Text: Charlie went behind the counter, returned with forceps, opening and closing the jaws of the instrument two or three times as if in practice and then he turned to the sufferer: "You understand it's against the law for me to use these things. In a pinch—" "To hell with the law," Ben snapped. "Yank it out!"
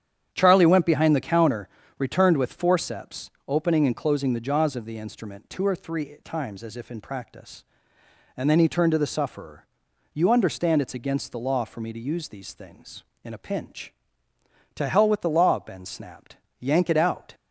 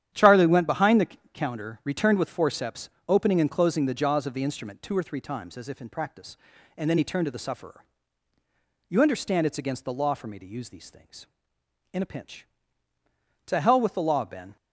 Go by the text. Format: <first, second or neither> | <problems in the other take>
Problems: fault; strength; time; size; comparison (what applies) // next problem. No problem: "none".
first | starts louder than the rest; strong; until 1.3 s; 10.5 dB; strong in the first // pauses between "the" and "counter"; slight; at 1.0 s; 0.24 s long // stops before "snapped Yank it out"; at 14.5 s